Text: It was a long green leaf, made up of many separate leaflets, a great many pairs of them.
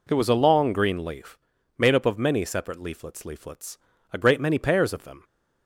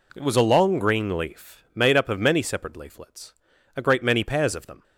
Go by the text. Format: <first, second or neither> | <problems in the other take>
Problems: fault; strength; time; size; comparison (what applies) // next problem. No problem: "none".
second | says "leaflets" twice; at 3.2 s